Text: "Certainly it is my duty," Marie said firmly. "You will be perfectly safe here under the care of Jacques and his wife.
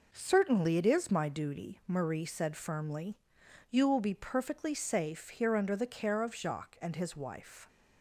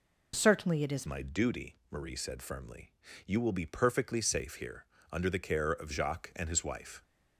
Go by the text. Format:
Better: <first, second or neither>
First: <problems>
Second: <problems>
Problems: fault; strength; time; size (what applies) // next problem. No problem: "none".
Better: first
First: none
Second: changes voice at "my"; from 1.0 s on; 6.0 s long // pauses between "here" and "under"; slight; at 4.8 s; 0.24 s long